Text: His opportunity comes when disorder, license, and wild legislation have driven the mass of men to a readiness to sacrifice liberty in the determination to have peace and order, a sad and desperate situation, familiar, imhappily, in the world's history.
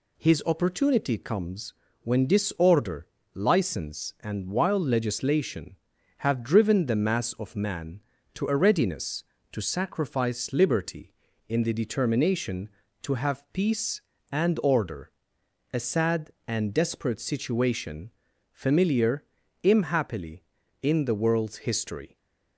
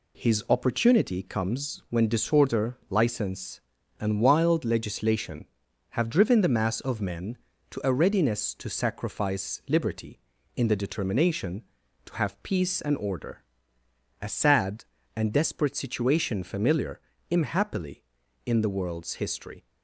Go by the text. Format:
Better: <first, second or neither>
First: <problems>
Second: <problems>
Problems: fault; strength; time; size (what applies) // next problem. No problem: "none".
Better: second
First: pauses between "comes" and "when"; slight; at 1.7 s; 0.30 s long // says "man" for "men"; at 7.5 s // stays silent after the last word; slight; from 22.0 s on; 0.5 s long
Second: none